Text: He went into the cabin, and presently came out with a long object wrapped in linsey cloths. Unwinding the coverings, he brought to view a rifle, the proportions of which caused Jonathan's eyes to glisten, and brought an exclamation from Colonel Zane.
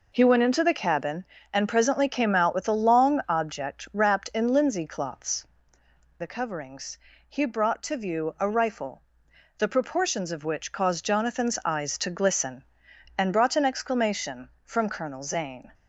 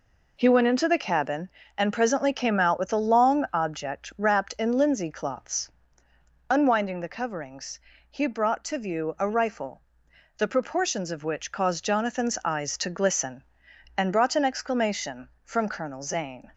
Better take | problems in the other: second | skips "Unwinding"; at 5.8 s

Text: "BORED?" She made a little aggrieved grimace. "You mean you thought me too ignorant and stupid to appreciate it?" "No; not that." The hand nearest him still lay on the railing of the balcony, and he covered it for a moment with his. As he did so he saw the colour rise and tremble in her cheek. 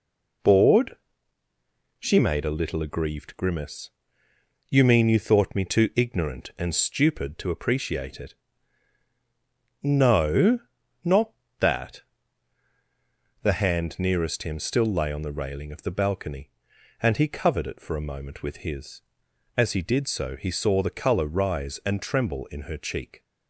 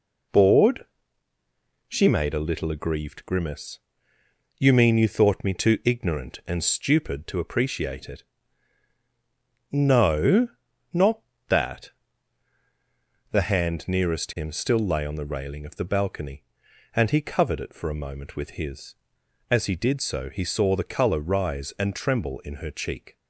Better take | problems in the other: neither | none

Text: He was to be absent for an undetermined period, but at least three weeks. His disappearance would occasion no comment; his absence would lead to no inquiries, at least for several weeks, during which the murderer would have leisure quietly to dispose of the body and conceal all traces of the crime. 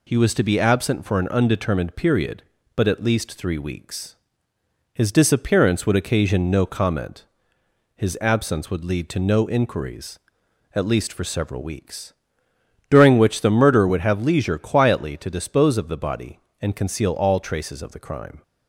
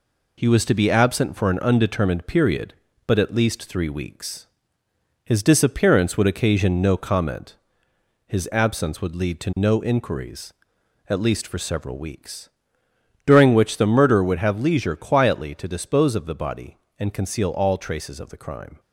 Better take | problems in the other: first | gets quieter; noticeable; throughout; 5 dB

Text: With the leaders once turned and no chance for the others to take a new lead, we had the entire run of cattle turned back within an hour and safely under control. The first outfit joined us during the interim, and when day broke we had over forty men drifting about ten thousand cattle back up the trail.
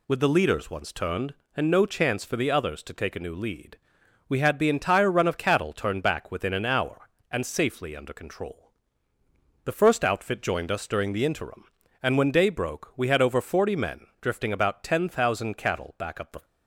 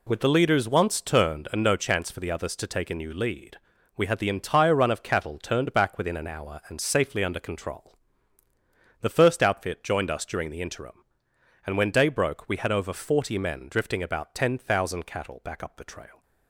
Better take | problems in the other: second | stops before "trail"; at 16.4 s

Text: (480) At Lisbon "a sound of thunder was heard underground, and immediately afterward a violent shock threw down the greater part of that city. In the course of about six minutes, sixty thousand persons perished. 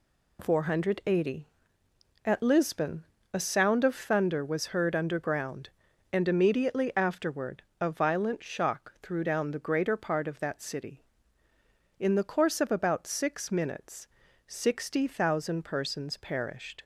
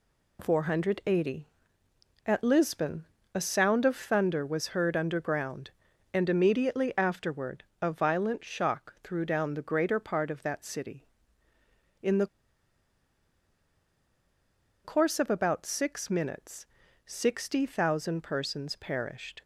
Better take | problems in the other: first | pauses between "Lisbon" and "a"; slight; at 3.0 s; 0.30 s long; slight in the first // pauses between "afterward" and "a"; slight; at 7.6 s; 0.20 s long; slight in the first // pauses between "the" and "course"; strong; at 12.2 s; 2.5 s long

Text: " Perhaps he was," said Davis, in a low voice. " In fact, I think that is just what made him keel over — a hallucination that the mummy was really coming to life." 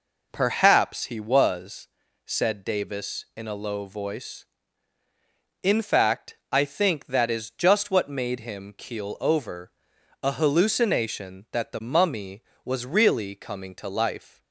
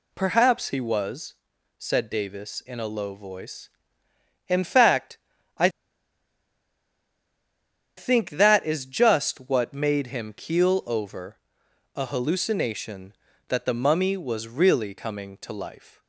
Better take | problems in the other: first | pauses between "I" and "think"; strong; at 5.6 s; 2.2 s long

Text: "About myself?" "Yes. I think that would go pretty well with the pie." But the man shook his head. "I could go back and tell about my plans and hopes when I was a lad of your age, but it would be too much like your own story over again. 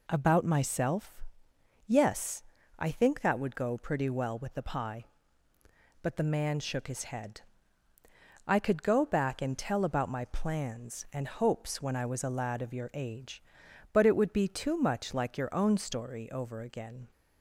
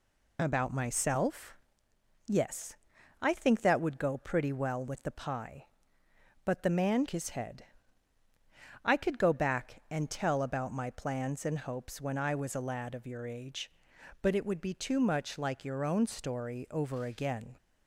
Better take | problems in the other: first | skips "shook"; at 7.0 s

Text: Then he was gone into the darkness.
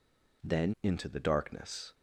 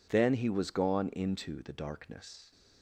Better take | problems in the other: second | skips "he was gone"; at 0.7 s

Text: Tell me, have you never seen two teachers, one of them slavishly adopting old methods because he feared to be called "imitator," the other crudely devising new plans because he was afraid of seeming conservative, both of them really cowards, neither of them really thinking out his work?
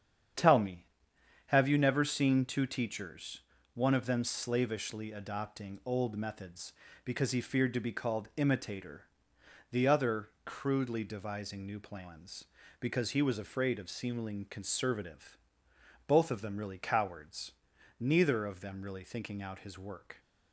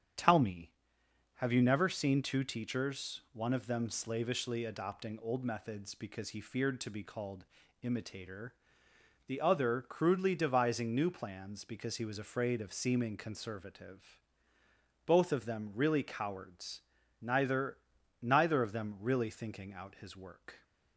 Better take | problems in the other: first | starts louder than the rest; strong; until 1.8 s; 8.5 dB; strong in the first // pauses between "called" and "imitator"; slight; at 7.4 s; 0.36 s long // says "neither" twice; at 18.2 s

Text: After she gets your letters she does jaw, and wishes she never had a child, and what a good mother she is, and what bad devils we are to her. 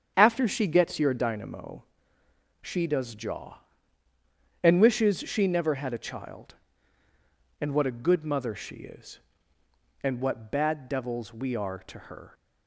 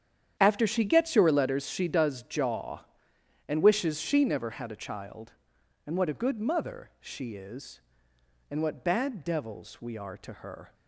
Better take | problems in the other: second | starts louder than the rest; strong; until 1.2 s; 8 dB; strong in the second // says "dynamo" for "letters"; at 1.1 s

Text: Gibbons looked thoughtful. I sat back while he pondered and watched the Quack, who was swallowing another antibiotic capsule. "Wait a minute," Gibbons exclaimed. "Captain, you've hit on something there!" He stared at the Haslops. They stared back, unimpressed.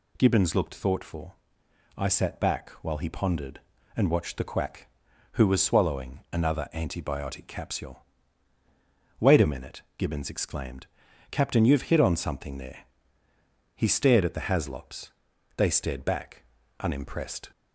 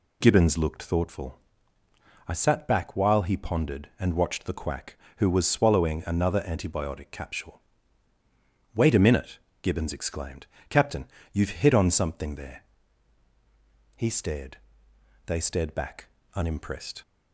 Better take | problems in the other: first | skips "at the Haslops"; at 14.9 s

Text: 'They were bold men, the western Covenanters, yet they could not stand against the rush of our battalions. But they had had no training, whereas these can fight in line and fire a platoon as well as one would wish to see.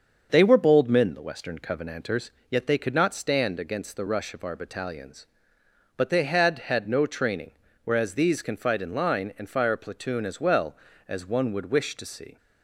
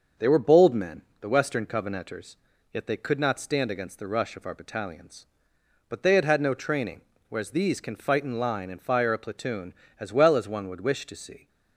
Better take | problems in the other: neither | starts louder than the rest; the same in both

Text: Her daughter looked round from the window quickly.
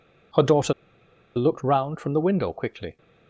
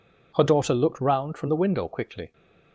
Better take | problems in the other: second | pauses between "daughter" and "looked"; noticeable; at 0.7 s; 0.64 s long

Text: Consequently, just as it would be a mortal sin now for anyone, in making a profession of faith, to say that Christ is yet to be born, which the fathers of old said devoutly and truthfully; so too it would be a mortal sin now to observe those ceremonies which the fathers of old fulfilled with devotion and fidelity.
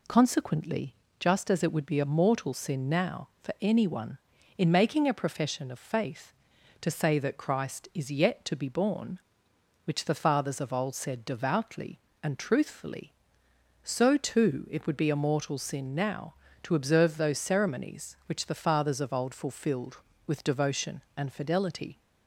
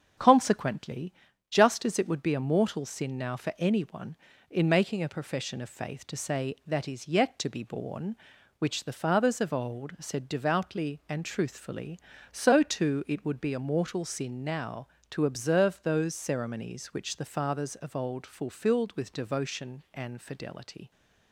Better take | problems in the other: first | starts louder than the rest; until 1.5 s; 7 dB // skips "Christ"; at 6.8 s

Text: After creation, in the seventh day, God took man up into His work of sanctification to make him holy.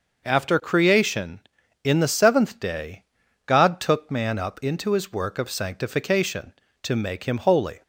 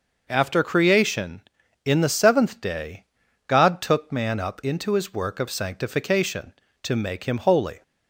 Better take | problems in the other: neither | none

